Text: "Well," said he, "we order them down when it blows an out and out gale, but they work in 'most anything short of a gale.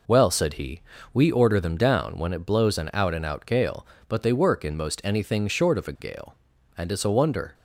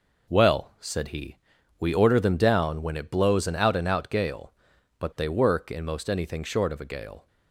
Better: second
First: goes on to say "And it's a wonder"; noticeable; from 6.7 s on; 0.76 s long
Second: none

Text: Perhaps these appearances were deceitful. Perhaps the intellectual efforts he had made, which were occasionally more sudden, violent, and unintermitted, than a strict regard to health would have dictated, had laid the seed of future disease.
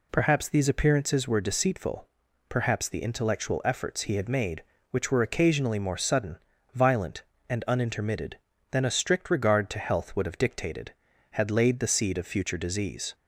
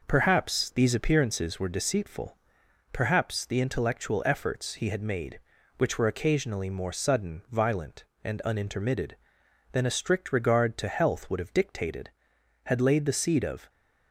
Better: first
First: none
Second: stops before "future disease"; at 13.6 s

